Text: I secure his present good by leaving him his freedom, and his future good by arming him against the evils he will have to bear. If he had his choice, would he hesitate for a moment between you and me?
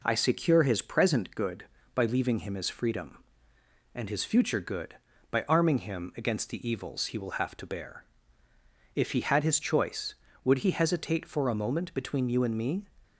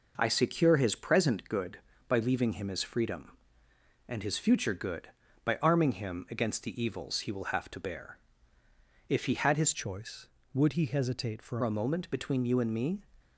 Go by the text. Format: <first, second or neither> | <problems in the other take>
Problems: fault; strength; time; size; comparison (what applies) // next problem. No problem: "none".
first | changes voice from "choice" to "for"; from 9.7 to 11.5 s; 1.8 s long